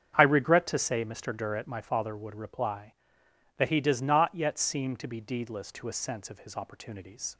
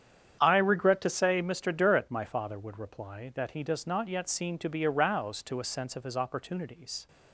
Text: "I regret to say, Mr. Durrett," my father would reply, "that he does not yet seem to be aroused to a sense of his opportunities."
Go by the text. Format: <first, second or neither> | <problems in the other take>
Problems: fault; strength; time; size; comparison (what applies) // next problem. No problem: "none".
second | starts louder than the rest; strong; until 1.1 s; 8 dB; strong in the second // says "deedless" for "aroused"; at 5.2 s